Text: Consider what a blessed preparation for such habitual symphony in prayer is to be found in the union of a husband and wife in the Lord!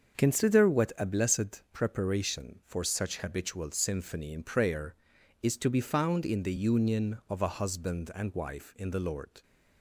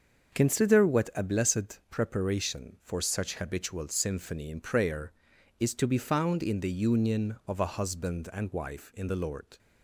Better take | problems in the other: neither | starts louder than the rest; the same in both

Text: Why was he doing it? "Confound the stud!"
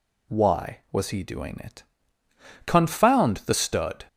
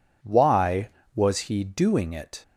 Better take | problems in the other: first | stops before "Confound the stud"; at 2.4 s

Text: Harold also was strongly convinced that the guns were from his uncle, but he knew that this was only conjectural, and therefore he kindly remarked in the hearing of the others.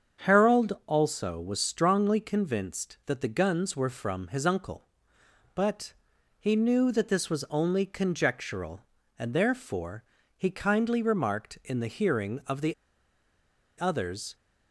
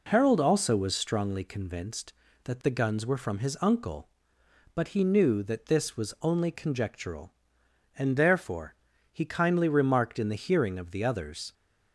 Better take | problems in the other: second | starts louder than the rest; strong; until 1.3 s; 7.5 dB // pauses between "but" and "he"; noticeable; at 5.9 s; 0.48 s long // pauses between "therefore" and "he"; slight; at 10.0 s; 0.32 s long; also in the second // pauses between "the" and "others"; at 12.7 s; 1.0 s long

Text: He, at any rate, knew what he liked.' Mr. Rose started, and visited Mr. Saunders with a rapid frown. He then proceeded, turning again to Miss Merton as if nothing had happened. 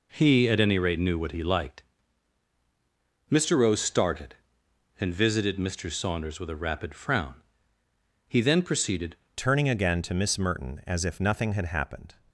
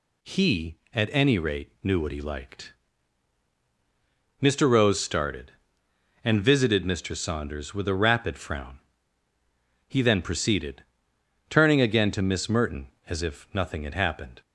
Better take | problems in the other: second | changes voice at "turning"; from 9.3 s on; 2.8 s long

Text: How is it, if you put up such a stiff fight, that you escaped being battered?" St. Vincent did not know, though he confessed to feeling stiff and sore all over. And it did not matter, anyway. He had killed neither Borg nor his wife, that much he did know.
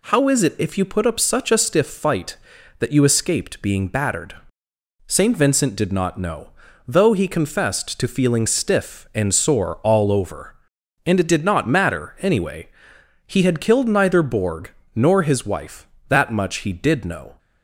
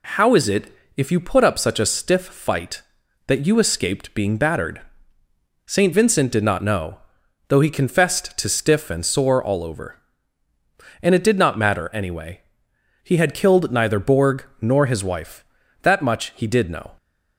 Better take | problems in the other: first | skips "feeling"; at 8.4 s // pauses between "Borg" and "nor"; slight; at 14.4 s; 0.16 s long; slight in the first

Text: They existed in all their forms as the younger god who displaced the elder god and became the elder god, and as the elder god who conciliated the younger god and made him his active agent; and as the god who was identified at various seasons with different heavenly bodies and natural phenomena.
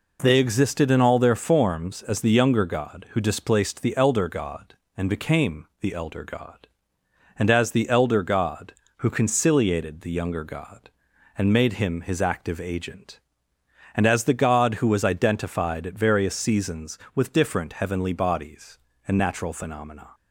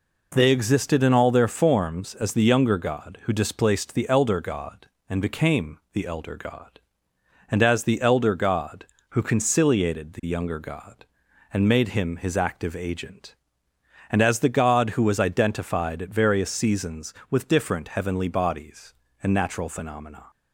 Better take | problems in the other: neither | pauses between "became" and "the"; slight; the same in both

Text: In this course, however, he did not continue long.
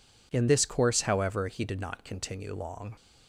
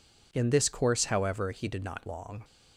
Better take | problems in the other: first | skips "continue"; at 2.0 s

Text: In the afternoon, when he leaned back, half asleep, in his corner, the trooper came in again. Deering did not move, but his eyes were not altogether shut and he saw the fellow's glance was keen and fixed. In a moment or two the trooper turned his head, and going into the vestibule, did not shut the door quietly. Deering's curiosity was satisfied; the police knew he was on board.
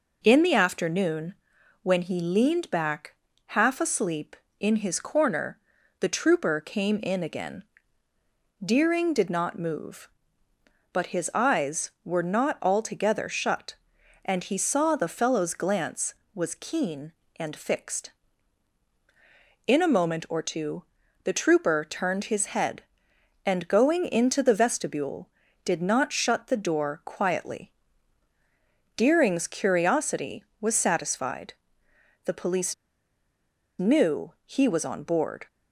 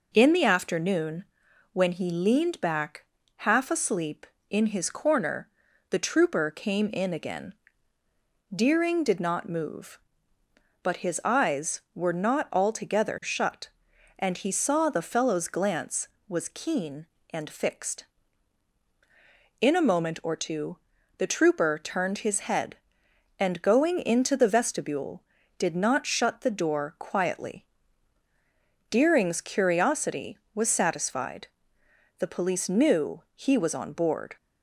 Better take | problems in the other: second | pauses between "two" and "the"; at 20.8 s; 0.40 s long; also in the second // pauses between "police" and "knew"; at 32.7 s; 1.0 s long

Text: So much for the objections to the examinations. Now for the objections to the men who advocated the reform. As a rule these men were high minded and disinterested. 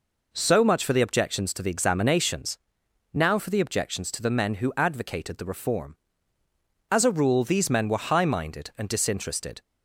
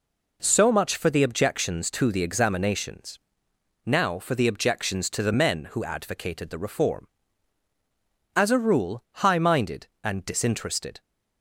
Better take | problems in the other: first | skips "these men were"; at 9.1 s

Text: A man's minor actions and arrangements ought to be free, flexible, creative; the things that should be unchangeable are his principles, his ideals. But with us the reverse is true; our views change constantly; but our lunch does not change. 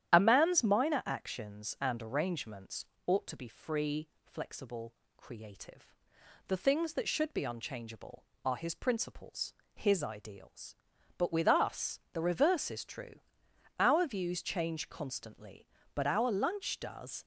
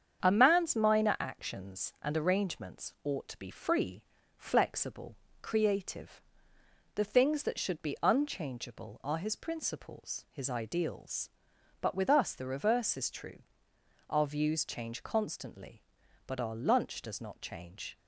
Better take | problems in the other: second | starts louder than the rest; strong; until 1.1 s; 11 dB; strong in the second // pauses between "arrangements" and "ought"; slight; at 2.8 s; 0.22 s long // stops before "not change"; at 17.2 s

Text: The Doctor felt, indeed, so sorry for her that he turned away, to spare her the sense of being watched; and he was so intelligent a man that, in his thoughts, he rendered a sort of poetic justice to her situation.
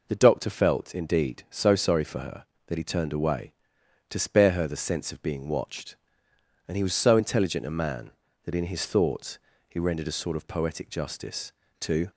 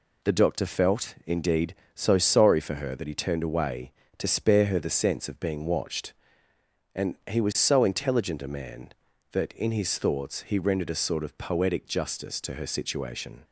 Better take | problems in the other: second | stops before "her situation"; at 12.1 s

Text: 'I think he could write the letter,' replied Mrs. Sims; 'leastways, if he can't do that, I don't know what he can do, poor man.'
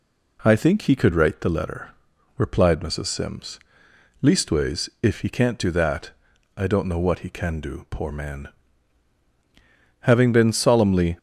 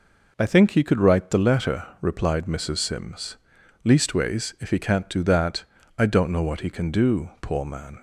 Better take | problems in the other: second | goes on to say "Having been solemnly"; noticeable; from 10.0 s on; 1.1 s long

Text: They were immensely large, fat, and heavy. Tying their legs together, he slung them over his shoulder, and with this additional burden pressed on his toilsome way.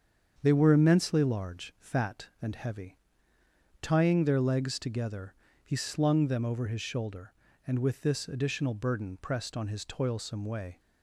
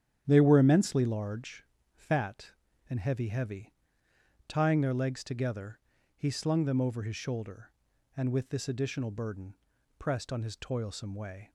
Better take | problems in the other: first | starts louder than the rest; strong; until 1.2 s; 9.5 dB; strong in the first // says "heavy" twice; at 3.2 s // pauses between "burden" and "pressed"; at 9.5 s; 0.42 s long

